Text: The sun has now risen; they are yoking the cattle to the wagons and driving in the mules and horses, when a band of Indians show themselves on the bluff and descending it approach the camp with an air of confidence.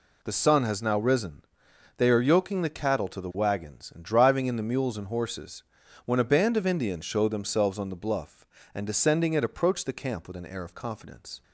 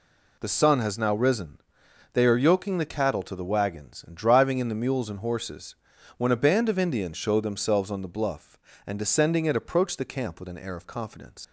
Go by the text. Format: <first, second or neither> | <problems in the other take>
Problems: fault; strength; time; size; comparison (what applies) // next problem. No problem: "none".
first | leaves "confidence" unfinished; at 11.4 s; 95 ms